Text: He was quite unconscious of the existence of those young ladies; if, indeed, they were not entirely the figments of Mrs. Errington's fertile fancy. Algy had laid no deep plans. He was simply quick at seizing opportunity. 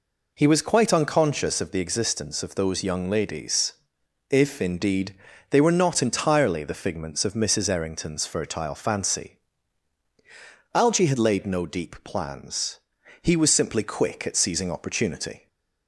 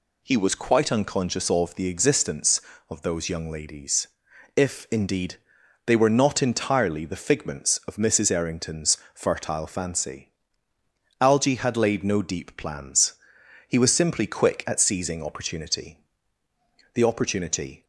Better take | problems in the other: first | pauses between "Errington's" and "fertile"; slight; at 8.9 s; 0.18 s long // goes on to say "The opportunity"; noticeable; from 16.9 s on; 0.90 s long

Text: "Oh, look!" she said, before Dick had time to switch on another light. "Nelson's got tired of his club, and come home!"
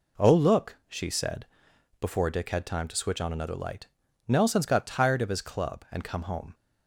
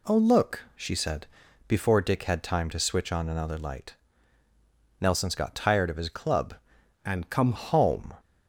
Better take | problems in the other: first | changes voice from "and" to "come"; from 7.0 to 7.5 s; 0.5 s long

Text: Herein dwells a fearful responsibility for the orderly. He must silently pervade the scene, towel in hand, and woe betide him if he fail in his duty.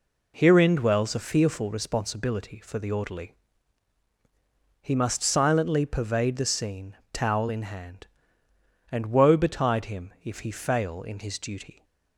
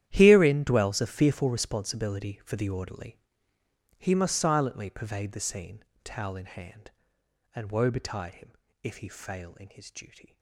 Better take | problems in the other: first | gets quieter; strong; throughout; 17.5 dB // pauses between "him" and "if"; slight; at 8.5 s; 0.30 s long

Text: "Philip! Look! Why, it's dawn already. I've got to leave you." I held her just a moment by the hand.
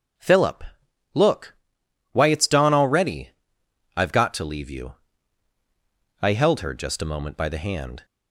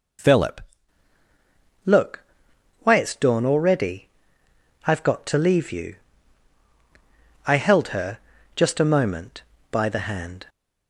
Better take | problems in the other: first | changes voice at "Look"; from 1.8 s on; 8.6 s long // pauses between "her" and "just"; slight; at 8.1 s; 0.36 s long

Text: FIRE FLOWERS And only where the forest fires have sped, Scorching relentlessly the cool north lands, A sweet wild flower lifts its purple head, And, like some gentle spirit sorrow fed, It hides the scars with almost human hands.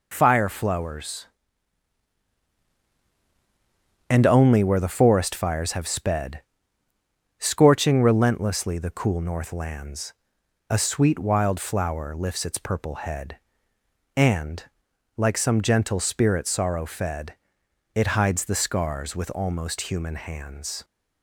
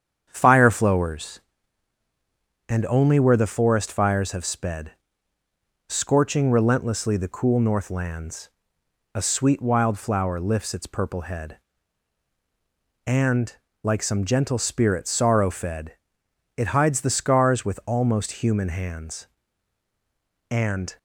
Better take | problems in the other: first | starts louder than the rest; strong; until 1.3 s; 8 dB // goes on to say "And"; slight; from 20.4 s on; 0.48 s long

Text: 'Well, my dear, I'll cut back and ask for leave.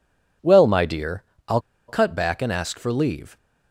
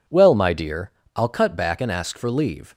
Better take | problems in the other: second | pauses between "I'll" and "cut"; slight; at 1.5 s; 0.28 s long

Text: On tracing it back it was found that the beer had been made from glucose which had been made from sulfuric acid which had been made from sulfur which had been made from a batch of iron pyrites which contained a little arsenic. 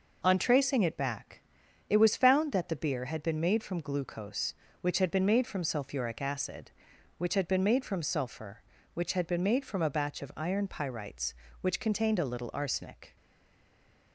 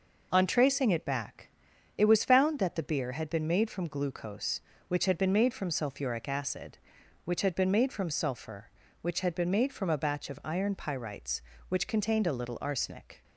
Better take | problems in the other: second | pauses between "back" and "it"; noticeable; at 1.4 s; 0.48 s long; noticeable in the second // stays silent after the last word; from 13.1 s on; 1.0 s long

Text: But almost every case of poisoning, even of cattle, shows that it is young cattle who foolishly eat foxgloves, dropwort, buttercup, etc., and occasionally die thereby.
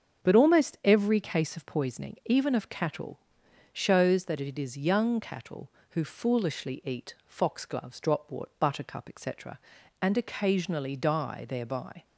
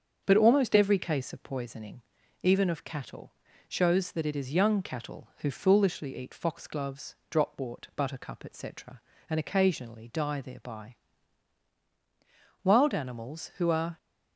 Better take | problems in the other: first | starts louder than the rest; until 1.2 s; 7 dB; strong in the first // goes on to say "Wild animals who are"; from 12.6 s on; 1.3 s long

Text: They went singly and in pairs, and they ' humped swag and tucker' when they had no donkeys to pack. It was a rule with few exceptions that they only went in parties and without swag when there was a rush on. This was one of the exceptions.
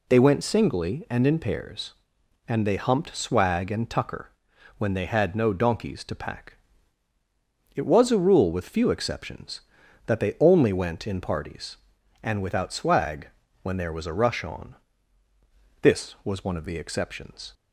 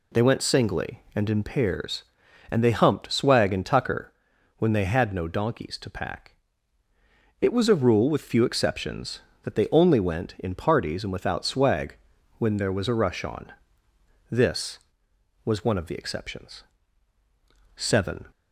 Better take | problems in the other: first | pauses between "tucker" and "when"; noticeable; at 4.1 s; 0.46 s long; noticeable in the first // pauses between "swag" and "when"; at 11.9 s; 0.42 s long; slight in the first // goes on to say "Seven"; from 17.7 s on; 0.54 s long

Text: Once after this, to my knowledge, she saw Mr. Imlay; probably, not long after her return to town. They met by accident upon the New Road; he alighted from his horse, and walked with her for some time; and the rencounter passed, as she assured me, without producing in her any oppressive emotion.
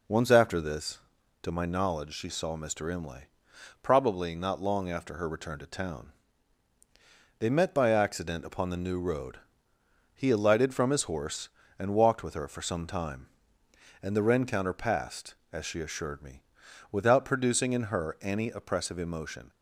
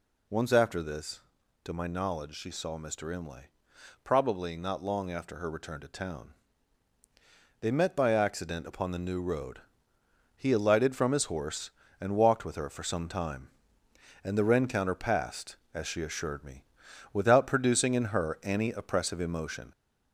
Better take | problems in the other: first | gets louder; slight; throughout; 2.5 dB

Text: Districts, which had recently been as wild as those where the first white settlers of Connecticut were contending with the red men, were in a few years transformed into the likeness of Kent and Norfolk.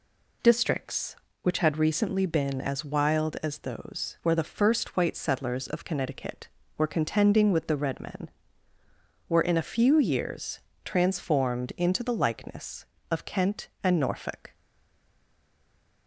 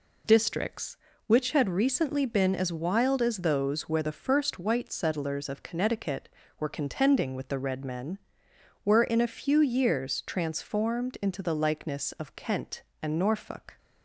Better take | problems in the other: second | pauses between "years" and "transformed"; slight; at 10.5 s; 0.26 s long // stays silent after the last word; noticeable; from 14.5 s on; 1.5 s long

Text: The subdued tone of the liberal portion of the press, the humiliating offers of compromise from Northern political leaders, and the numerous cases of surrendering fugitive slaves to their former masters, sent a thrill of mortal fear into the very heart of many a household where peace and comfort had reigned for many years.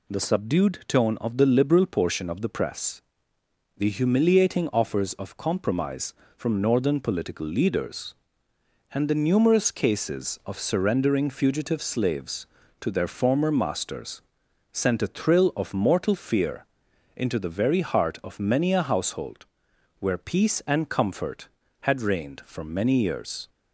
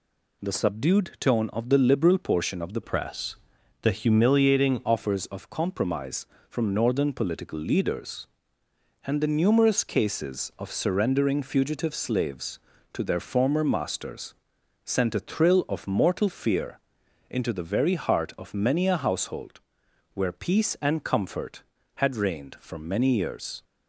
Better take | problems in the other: first | changes voice from "press" to "humiliating"; from 2.8 to 4.8 s; 2.0 s long // pauses between "fear" and "into"; noticeable; at 16.7 s; 0.50 s long; noticeable in the first // pauses between "household" and "where"; noticeable; at 19.5 s; 0.54 s long; noticeable in the first

